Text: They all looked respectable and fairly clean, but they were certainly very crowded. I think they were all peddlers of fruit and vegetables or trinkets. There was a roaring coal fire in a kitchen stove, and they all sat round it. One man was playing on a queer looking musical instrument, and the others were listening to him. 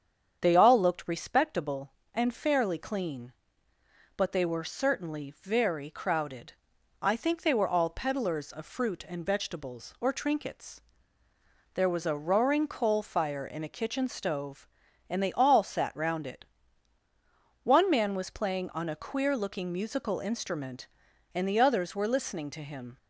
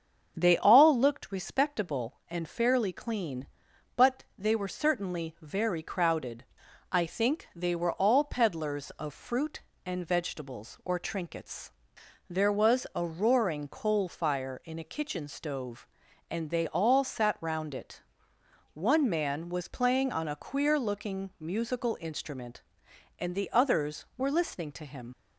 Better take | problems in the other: first | starts louder than the rest; until 1.3 s; 7 dB; strong in the first // leaves "him" unfinished; at 25.1 s; 45 ms

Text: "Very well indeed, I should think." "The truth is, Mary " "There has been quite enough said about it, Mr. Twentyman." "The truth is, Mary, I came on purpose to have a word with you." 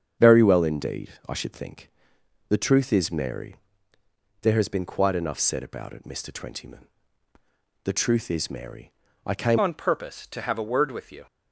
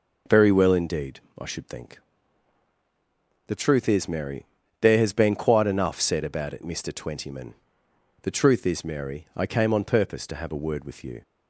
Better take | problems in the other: second | starts louder than the rest; strong; until 1.3 s; 7.5 dB // changes voice at "on"; from 9.6 s on; 1.6 s long

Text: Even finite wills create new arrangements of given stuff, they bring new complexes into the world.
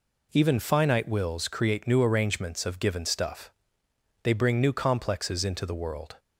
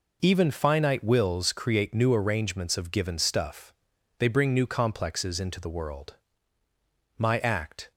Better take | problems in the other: first | goes on to say "My act"; noticeable; from 7.1 s on; 0.74 s long

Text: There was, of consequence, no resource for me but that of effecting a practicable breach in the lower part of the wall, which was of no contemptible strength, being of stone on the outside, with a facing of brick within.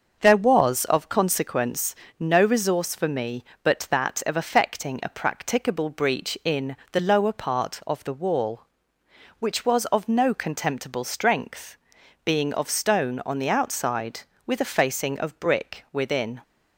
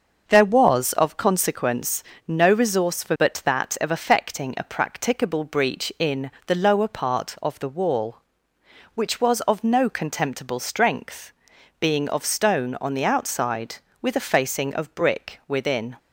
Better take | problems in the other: first | starts louder than the rest; until 1.2 s; 6.5 dB; noticeable in the first // skips "me"; at 3.1 s // pauses between "in" and "the"; slight; at 6.2 s; 0.16 s long; slight in the first

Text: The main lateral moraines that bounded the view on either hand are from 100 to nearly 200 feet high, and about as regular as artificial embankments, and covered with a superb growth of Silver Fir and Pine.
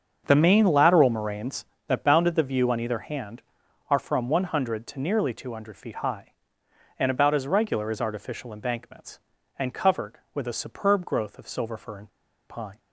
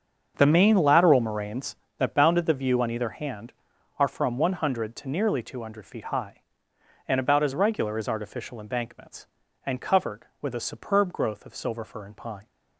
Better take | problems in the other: second | starts louder than the rest; until 1.2 s; 7 dB; also in the second // pauses between "and" and "Pine"; at 12.0 s; 0.40 s long

